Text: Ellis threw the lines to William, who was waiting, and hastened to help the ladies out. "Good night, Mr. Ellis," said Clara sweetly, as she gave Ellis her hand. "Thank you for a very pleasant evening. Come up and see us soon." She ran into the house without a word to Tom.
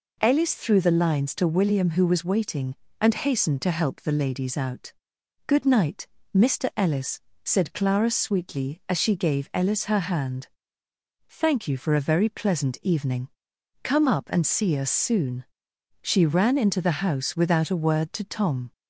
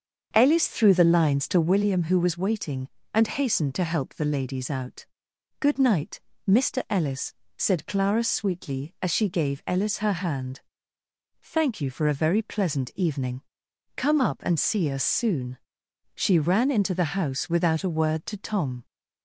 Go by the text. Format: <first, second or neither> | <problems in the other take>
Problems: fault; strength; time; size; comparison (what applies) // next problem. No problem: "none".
first | starts louder than the rest; until 1.9 s; 7 dB